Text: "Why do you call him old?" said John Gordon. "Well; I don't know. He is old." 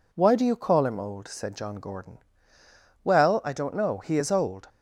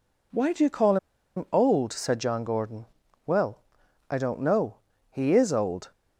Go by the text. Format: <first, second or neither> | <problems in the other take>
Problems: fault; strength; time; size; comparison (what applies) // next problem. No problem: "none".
first | pauses between "call" and "him"; at 0.9 s; 0.40 s long